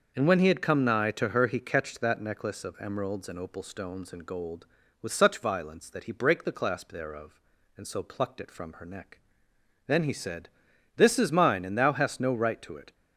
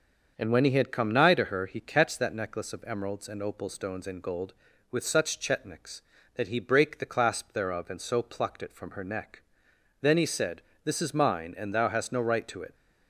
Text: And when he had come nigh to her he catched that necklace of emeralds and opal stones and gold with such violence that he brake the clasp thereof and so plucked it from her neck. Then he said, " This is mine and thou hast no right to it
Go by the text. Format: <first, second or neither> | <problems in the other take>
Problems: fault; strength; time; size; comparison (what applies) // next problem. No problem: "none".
first | starts louder than the rest; until 1.3 s; 6.5 dB; also in the first // says "chetniks" for "violence"; at 5.3 s